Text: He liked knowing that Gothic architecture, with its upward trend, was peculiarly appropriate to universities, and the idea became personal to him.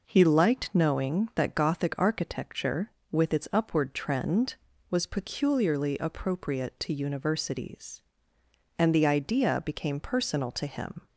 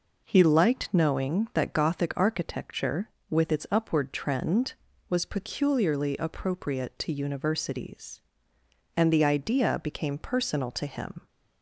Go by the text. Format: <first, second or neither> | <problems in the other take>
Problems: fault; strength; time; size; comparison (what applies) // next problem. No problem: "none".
neither | none